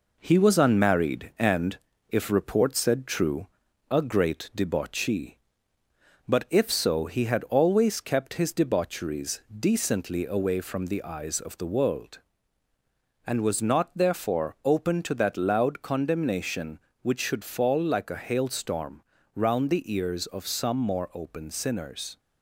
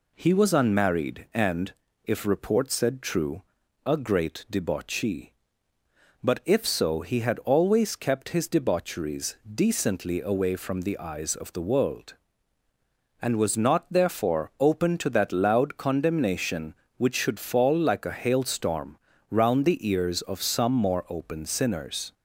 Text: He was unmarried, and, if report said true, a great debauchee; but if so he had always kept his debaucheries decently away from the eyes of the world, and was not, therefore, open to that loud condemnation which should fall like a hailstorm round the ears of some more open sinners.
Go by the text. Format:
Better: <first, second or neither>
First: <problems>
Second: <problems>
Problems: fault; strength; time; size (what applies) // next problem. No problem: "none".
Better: second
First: gets quieter; slight; throughout; 3 dB // pauses between "hailstorm" and "round"; slight; at 19.0 s; 0.34 s long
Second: pauses between "hailstorm" and "round"; slight; at 18.9 s; 0.34 s long